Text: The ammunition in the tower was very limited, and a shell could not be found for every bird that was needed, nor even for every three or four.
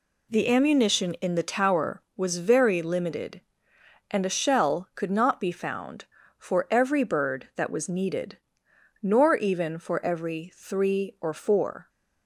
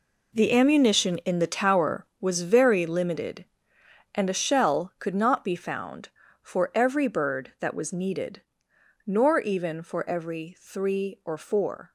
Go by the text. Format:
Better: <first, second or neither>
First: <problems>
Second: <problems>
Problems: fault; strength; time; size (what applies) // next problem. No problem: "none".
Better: first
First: none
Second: gets quieter; strong; throughout; 12.5 dB